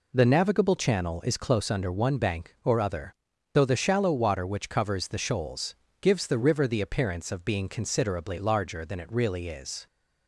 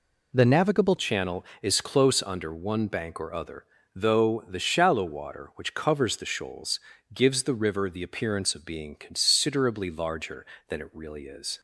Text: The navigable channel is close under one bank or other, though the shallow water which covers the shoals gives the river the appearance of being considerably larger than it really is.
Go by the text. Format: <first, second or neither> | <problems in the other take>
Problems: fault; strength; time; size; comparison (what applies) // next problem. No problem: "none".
first | changes voice at "channel"; from 0.9 s on; 10.6 s long // pauses between "shoals" and "gives"; slight; at 6.7 s; 0.34 s long; slight in the first